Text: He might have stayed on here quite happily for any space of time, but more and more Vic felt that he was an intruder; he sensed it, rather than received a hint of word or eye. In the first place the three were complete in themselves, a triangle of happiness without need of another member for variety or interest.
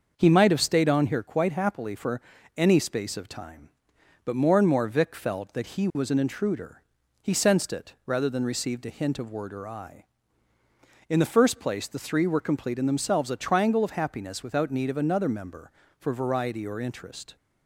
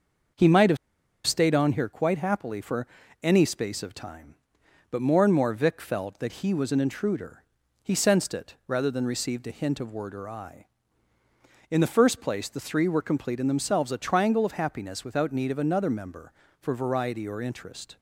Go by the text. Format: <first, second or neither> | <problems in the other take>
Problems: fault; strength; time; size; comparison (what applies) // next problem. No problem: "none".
first | starts louder than the rest; until 1.8 s; 6.5 dB; also in the first // pauses between "have" and "stayed"; noticeable; at 0.7 s; 0.49 s long // pauses between "for" and "any"; slight; at 2.8 s; 0.34 s long; slight in the first